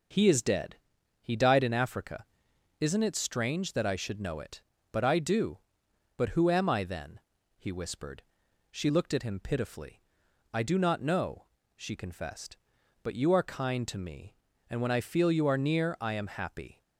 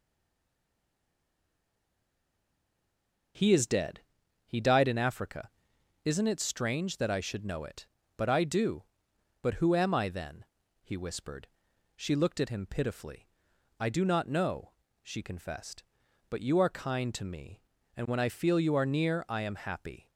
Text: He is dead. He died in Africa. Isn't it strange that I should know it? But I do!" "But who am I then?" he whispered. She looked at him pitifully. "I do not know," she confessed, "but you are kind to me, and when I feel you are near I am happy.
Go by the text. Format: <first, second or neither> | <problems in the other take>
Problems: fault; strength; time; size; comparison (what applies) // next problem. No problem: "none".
first | stays silent before the first word; strong; until 3.3 s; 3.3 s long